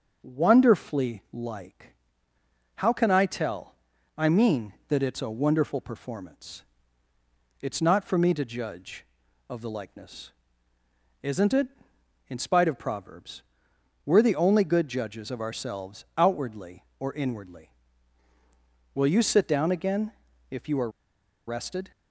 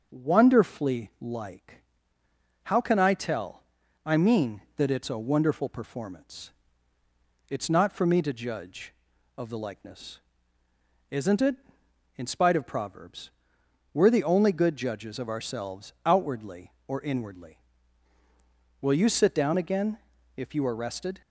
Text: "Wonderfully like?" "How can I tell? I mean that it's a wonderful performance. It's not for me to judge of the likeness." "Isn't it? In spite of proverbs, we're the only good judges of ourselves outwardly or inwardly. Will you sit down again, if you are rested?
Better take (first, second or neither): second